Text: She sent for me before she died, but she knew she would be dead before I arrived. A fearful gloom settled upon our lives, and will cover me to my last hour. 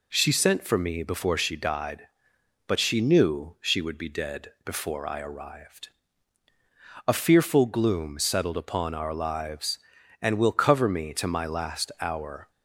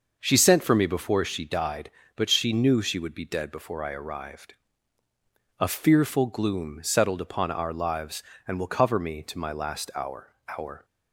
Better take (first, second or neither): first